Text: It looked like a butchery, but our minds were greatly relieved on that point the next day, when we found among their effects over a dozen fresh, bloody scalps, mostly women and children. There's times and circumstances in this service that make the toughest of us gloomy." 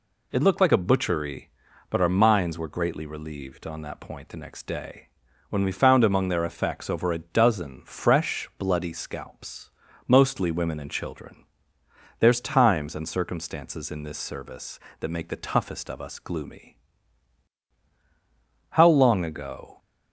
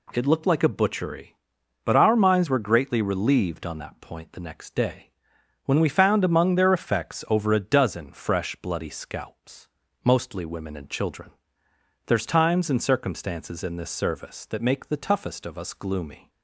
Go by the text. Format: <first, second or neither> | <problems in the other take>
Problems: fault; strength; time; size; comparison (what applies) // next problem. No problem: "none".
second | goes on to say "How long ago"; noticeable; from 18.7 s on; 1.0 s long